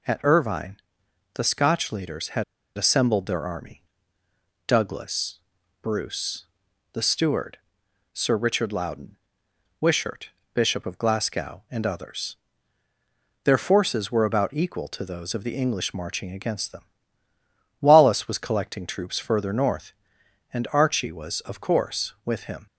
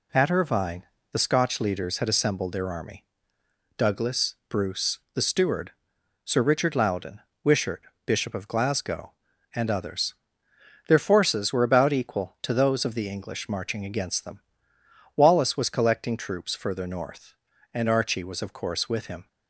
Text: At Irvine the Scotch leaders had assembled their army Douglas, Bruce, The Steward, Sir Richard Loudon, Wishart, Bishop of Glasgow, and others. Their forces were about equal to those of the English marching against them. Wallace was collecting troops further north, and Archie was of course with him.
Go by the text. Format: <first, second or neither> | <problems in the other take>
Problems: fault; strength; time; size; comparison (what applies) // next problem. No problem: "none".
second | pauses between "Irvine" and "the"; noticeable; at 0.7 s; 0.56 s long; slight in the second // pauses between "had" and "assembled"; slight; at 2.4 s; 0.32 s long // pauses between "army" and "Douglas"; noticeable; at 3.8 s; 0.82 s long; noticeable in the second